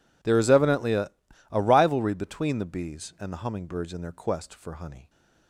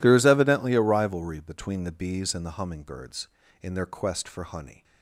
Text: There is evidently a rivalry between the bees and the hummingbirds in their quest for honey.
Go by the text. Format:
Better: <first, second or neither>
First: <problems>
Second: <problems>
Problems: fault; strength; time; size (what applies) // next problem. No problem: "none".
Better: second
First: says "a" twice; at 1.5 s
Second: none